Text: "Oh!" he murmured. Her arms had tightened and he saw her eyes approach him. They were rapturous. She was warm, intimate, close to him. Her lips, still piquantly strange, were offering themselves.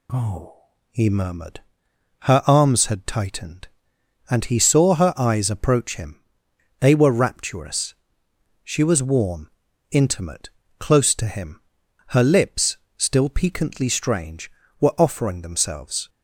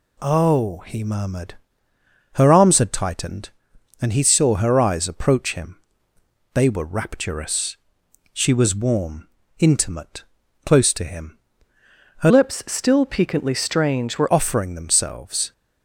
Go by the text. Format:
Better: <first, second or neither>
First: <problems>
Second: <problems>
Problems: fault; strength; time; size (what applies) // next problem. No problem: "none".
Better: first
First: none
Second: changes voice from "lips" to "were"; from 12.2 to 14.3 s; 2.1 s long